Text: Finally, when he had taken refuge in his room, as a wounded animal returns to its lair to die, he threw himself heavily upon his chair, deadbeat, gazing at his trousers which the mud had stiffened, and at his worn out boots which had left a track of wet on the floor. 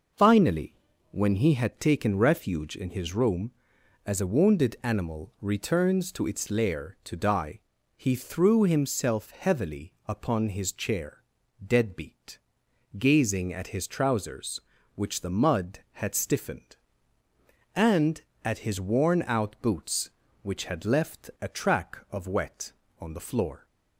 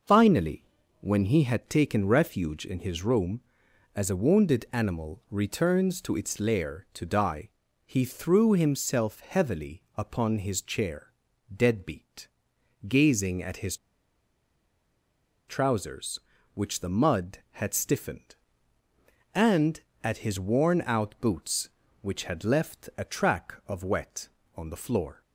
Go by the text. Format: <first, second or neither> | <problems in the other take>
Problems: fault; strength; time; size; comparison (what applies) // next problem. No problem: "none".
first | pauses between "his" and "trousers"; strong; at 13.7 s; 1.7 s long